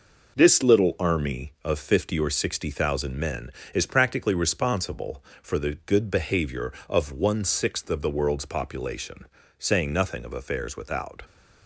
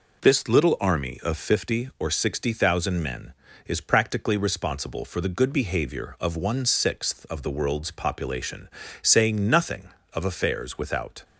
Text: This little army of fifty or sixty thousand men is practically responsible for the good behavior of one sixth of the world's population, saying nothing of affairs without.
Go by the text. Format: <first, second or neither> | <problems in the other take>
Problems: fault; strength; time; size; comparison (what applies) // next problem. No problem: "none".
neither | none